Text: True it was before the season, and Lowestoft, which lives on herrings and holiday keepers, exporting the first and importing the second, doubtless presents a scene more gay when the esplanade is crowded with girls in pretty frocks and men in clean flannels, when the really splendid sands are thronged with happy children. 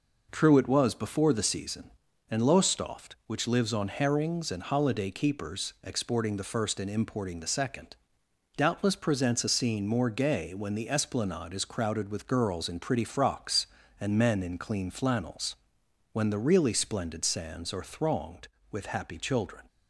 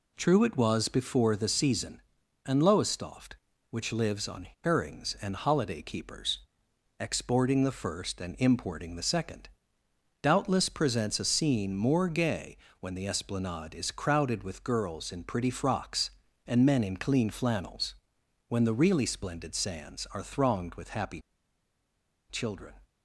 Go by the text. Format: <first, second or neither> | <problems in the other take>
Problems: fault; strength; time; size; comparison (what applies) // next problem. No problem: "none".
first | pauses between "on" and "herrings"; slight; at 4.4 s; 0.16 s long // pauses between "gay" and "when"; slight; at 12.5 s; 0.24 s long // pauses between "happy" and "children"; at 21.1 s; 1.1 s long